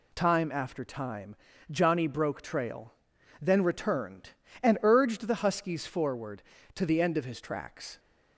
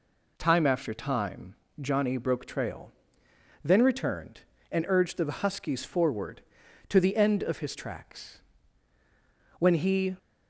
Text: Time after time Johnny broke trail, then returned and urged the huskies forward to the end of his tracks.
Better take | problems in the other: first | pauses between "time" and "Johnny"; slight; at 1.5 s; 0.26 s long; slight in the first // goes on to say "When he"; from 9.5 s on; 0.56 s long

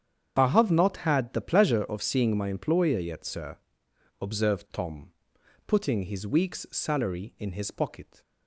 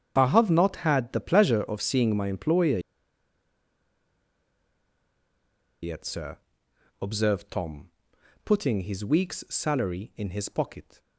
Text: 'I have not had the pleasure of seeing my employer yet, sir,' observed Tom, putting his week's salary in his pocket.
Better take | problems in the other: first | starts louder than the rest; strong; until 1.1 s; 8 dB; strong in the first // pauses between "employer" and "yet"; strong; at 2.7 s; 3.0 s long

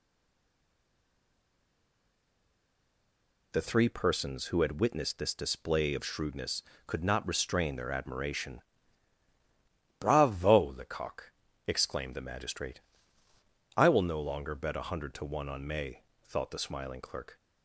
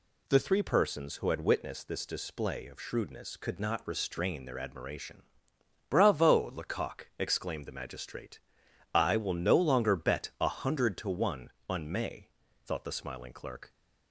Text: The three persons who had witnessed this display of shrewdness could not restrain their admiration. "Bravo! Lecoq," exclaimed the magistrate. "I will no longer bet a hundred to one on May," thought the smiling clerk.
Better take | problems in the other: second | stays silent before the first word; strong; until 3.5 s; 3.5 s long

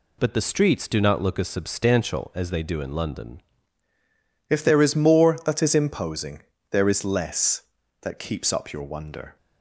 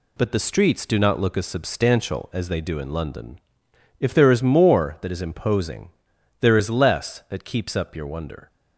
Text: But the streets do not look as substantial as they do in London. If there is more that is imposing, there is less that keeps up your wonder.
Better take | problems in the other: second | changes voice at "If"; from 4.4 s on; 4.9 s long

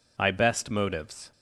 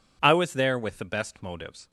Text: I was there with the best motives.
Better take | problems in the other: second | skips "was there with the"; at 0.2 s

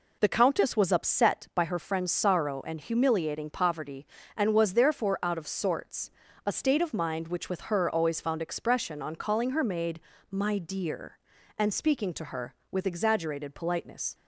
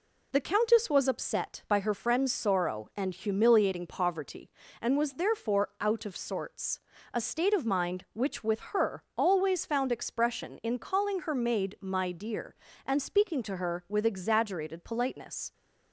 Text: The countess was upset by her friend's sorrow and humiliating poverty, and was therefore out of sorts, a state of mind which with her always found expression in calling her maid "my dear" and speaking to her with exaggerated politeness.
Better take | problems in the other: second | says "on" for "in"; at 9.0 s // pauses between "maid" and "my"; slight; at 9.9 s; 0.32 s long

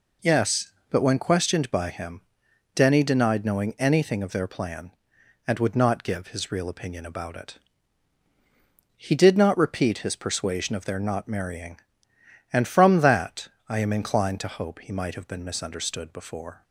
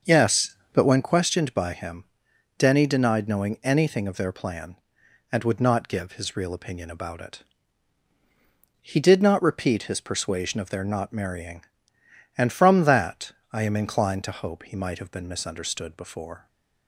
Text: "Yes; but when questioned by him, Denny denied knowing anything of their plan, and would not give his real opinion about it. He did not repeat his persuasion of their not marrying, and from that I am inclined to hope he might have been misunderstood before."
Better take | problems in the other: first | starts louder than the rest; until 1.1 s; 6.5 dB // pauses between "that" and "I"; slight; at 13.3 s; 0.18 s long; slight in the first

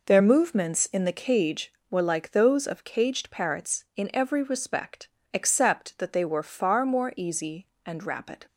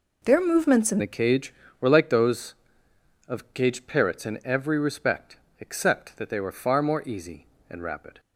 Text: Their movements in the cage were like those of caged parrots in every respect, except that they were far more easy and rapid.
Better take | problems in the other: first | changes voice at "the"; from 0.9 s on; 7.2 s long

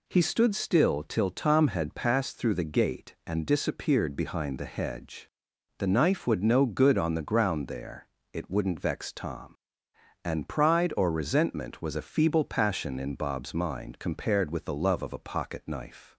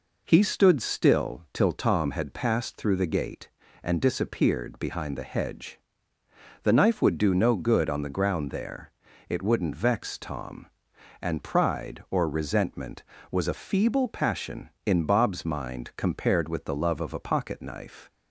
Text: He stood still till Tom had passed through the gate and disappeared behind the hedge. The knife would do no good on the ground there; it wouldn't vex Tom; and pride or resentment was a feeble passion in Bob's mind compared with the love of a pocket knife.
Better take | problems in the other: second | skips "do"; at 6.4 s

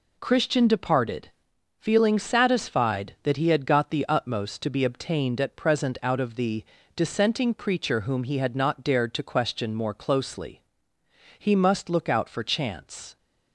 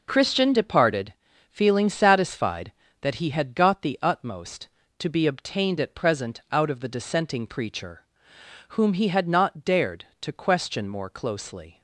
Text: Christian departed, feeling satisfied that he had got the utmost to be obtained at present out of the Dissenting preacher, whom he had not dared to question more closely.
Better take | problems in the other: second | pauses between "the" and "Dissenting"; slight; at 6.6 s; 0.32 s long // goes on to say "He must look out for chance"; strong; from 11.3 s on; 1.8 s long

